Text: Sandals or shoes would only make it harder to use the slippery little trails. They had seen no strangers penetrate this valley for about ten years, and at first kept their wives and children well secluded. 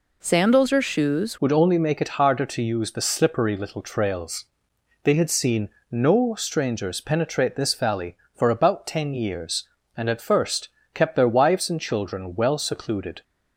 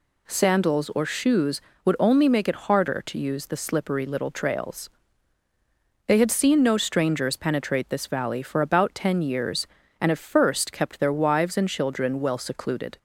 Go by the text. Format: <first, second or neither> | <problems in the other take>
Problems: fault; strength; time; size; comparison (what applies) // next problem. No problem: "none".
second | changes voice at "would"; from 1.4 s on; 11.8 s long // pauses between "seen" and "no"; slight; at 5.6 s; 0.22 s long // pauses between "first" and "kept"; slight; at 10.6 s; 0.24 s long